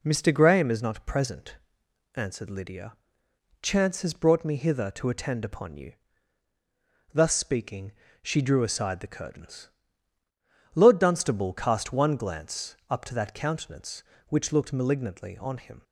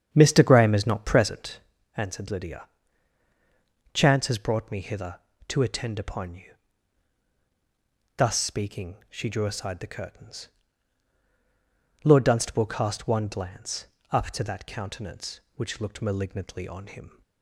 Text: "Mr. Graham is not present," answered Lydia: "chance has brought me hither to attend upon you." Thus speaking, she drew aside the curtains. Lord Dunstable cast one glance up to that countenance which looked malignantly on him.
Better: first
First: none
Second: starts louder than the rest; strong; until 1.6 s; 8 dB // pauses between "glance" and "up"; slight; at 13.8 s; 0.24 s long

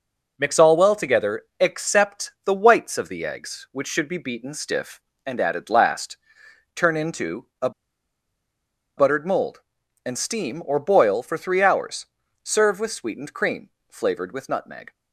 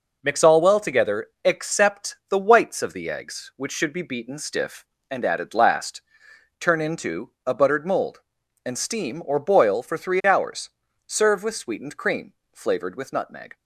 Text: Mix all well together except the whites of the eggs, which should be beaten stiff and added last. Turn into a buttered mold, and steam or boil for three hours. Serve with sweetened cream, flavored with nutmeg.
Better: second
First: pauses between "together" and "except"; slight; at 1.4 s; 0.16 s long // pauses between "into" and "a"; slight; at 7.4 s; 0.16 s long // pauses between "a" and "buttered"; strong; at 7.6 s; 1.2 s long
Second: pauses between "together" and "except"; slight; at 1.2 s; 0.16 s long // pauses between "into" and "a"; slight; at 7.3 s; 0.16 s long

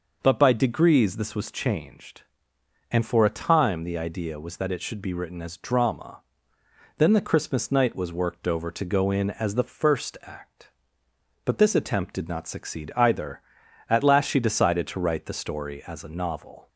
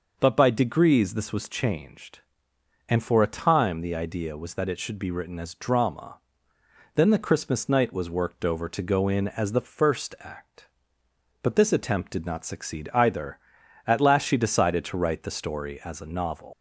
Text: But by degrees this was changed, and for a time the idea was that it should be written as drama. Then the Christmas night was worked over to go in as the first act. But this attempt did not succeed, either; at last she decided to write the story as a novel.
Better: first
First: none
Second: leaves "novel" unfinished; at 16.5 s; 120 ms

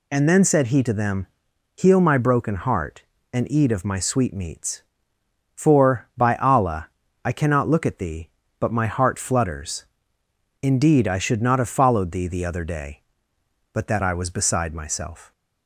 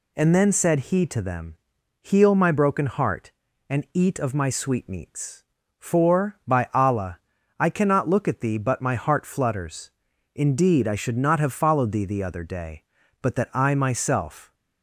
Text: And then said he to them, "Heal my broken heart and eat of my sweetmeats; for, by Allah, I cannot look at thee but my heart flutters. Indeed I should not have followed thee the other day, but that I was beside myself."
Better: first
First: none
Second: skips "was beside"; at 13.7 s

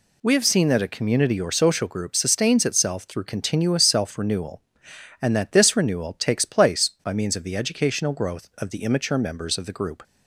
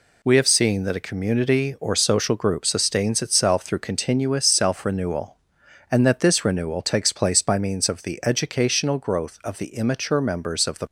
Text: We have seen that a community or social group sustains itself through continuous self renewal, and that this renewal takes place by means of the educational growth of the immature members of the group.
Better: first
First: none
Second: stops before "group"; at 10.8 s

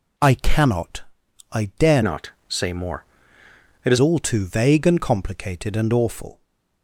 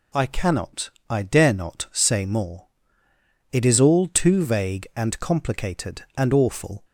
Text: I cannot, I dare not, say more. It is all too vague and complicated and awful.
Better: second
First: changes voice from "not" to "is"; from 2.0 to 3.9 s; 1.9 s long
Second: none

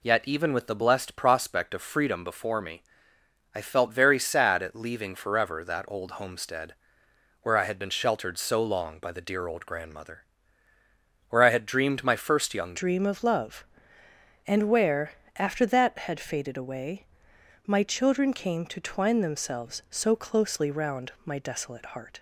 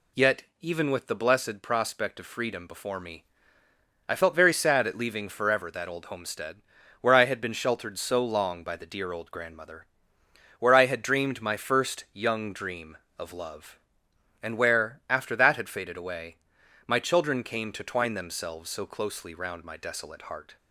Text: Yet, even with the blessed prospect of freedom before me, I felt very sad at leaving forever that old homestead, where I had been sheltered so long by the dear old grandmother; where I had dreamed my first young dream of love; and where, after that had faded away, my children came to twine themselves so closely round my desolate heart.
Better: second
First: changes voice at "dream"; from 12.7 s on; 9.4 s long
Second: none

